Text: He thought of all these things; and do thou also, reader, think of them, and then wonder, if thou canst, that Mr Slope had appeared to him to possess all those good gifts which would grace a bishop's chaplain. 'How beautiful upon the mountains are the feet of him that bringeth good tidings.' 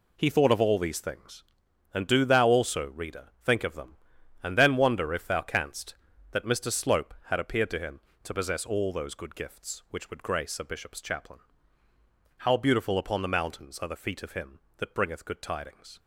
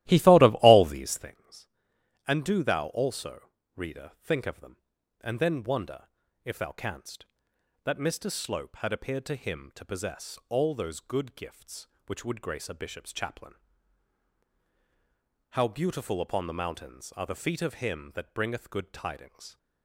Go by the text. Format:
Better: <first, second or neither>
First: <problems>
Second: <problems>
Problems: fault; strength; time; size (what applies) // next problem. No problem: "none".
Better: first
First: none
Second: starts louder than the rest; strong; until 1.4 s; 15 dB